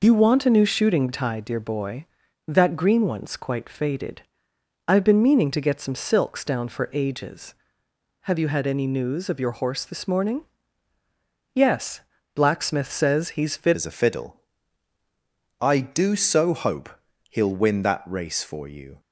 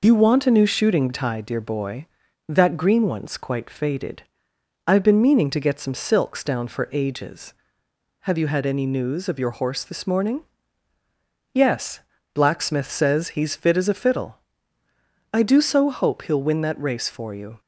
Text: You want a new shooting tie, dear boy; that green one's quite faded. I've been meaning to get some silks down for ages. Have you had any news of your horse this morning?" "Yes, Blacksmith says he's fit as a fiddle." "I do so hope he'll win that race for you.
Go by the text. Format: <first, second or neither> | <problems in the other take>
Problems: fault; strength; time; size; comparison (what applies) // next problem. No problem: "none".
second | changes voice at "as"; from 13.7 s on; 5.2 s long // pauses between "hope" and "he'll"; at 16.8 s; 0.42 s long